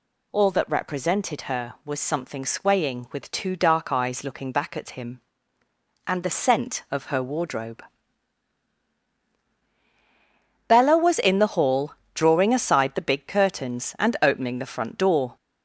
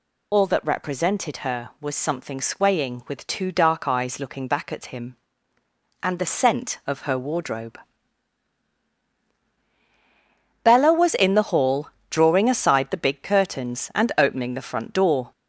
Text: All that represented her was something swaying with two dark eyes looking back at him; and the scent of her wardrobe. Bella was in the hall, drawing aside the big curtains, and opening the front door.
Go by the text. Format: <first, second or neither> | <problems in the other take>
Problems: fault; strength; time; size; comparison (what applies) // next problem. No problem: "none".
first | loses the start of "All"; at 0.3 s; 45 ms